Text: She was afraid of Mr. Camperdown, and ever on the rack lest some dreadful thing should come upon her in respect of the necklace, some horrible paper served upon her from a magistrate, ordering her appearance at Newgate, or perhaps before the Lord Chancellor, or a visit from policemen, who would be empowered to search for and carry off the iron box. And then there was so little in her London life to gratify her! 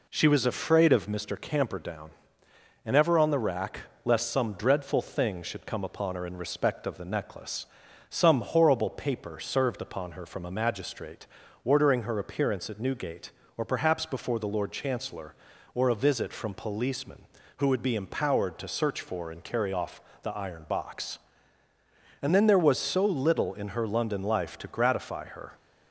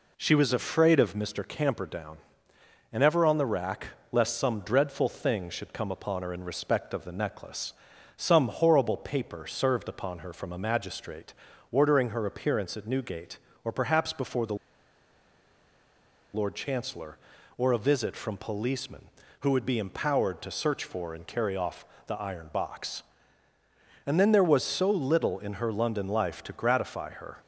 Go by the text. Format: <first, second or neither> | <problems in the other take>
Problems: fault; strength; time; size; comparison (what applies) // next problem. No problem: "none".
first | pauses between "rack" and "lest"; slight; at 3.8 s; 0.24 s long; slight in the first // pauses between "the" and "Lord"; strong; at 14.5 s; 1.7 s long // pauses between "off" and "the"; slight; at 21.8 s; 0.22 s long; slight in the first